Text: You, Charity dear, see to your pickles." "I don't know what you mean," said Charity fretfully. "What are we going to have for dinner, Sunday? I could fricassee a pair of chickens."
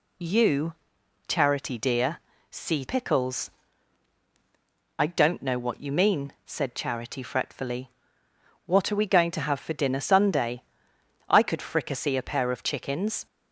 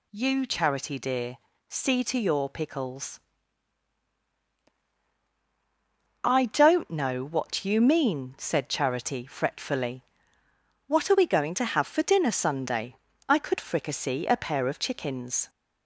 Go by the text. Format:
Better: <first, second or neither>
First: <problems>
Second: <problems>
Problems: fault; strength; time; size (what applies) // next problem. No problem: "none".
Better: second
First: skips "to your"; at 2.8 s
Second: none